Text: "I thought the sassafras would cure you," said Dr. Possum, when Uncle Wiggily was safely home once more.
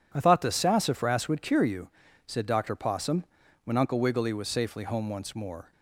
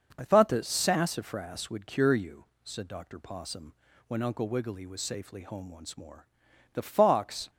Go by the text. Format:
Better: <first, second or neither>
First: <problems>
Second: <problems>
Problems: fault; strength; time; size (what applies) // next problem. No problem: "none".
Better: first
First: none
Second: starts louder than the rest; until 1.1 s; 6 dB // goes on to say "The fox"; noticeable; from 6.7 s on; 0.76 s long